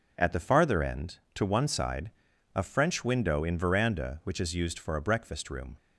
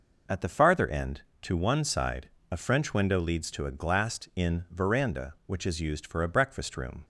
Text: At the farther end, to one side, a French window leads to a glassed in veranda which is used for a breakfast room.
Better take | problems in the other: second | skips "leads to a glassed"; at 3.4 s

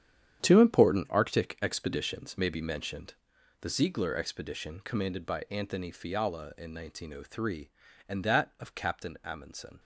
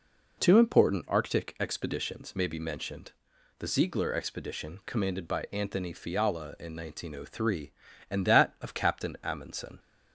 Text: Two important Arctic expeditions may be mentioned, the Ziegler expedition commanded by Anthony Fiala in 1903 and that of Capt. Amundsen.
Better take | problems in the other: second | gets quieter; strong; throughout; 11 dB

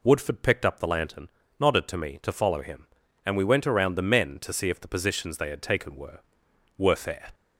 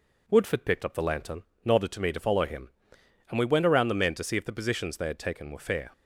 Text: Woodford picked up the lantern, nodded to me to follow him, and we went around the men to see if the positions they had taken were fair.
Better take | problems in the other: second | says "were" twice; at 6.7 s

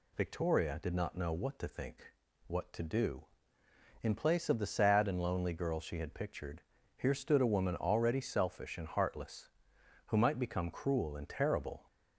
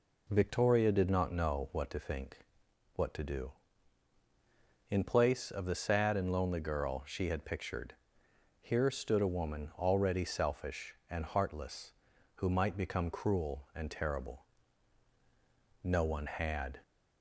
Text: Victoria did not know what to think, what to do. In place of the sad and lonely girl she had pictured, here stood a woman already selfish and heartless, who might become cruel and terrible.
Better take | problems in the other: first | goes on to say "No one had"; noticeable; from 15.8 s on; 0.98 s long

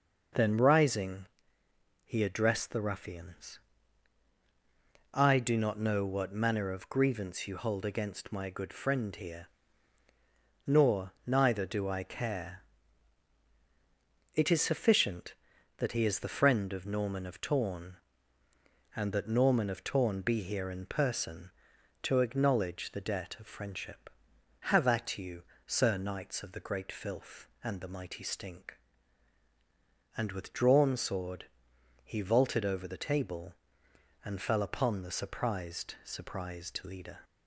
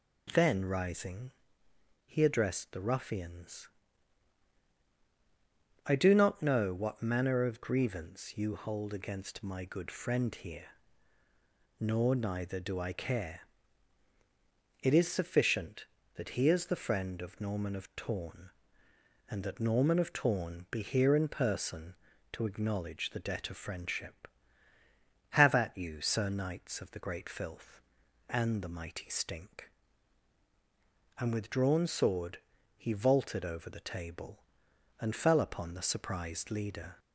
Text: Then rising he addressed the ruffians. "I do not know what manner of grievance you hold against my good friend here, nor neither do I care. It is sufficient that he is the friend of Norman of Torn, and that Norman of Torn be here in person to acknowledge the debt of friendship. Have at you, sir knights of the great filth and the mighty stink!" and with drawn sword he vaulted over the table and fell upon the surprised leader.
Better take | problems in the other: second | pauses between "rising" and "he"; noticeable; at 1.2 s; 0.78 s long; noticeable in the second // pauses between "sword" and "he"; noticeable; at 31.4 s; 0.58 s long; slight in the second // says "surprised" twice; at 36.0 s

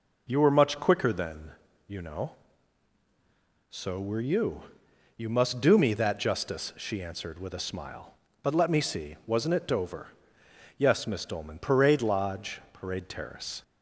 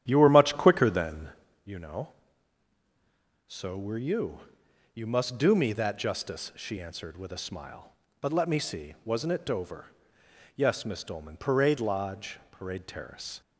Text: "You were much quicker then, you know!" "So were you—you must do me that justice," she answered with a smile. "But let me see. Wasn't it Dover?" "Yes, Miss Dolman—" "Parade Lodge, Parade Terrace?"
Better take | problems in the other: first | starts louder than the rest; strong; until 1.6 s; 10.5 dB

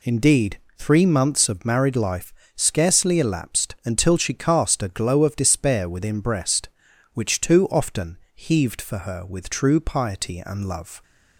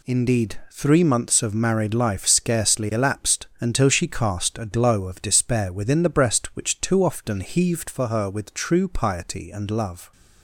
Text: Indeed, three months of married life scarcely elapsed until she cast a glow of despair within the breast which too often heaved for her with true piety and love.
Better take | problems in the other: second | pauses between "life" and "scarcely"; slight; at 2.3 s; 0.22 s long // skips "the"; at 6.2 s // pauses between "often" and "heaved"; slight; at 8.1 s; 0.18 s long

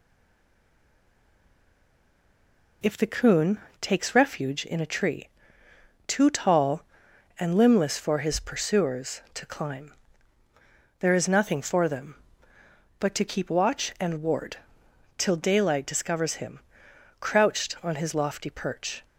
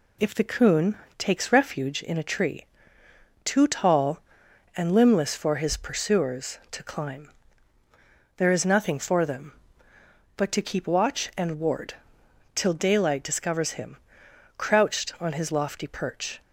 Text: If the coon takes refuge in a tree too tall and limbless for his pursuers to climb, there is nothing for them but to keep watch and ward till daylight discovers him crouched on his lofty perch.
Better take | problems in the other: second | stays silent before the first word; strong; until 2.8 s; 2.8 s long // pauses between "coon" and "takes"; slight; at 3.6 s; 0.20 s long; slight in the second // pauses between "tree" and "too"; noticeable; at 5.2 s; 0.80 s long; noticeable in the second // pauses between "ward" and "till"; noticeable; at 14.5 s; 0.60 s long; noticeable in the second // pauses between "him" and "crouched"; noticeable; at 16.5 s; 0.62 s long; noticeable in the second

